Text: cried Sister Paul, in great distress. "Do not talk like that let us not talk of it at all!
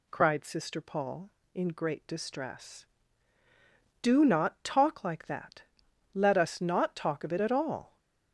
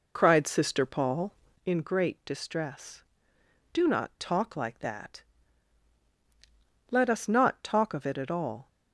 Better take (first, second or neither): first